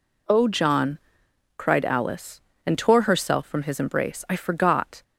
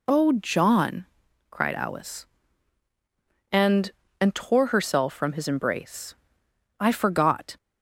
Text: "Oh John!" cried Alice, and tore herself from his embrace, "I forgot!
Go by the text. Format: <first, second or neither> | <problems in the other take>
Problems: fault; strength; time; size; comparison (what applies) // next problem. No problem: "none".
first | says "and" twice; at 4.2 s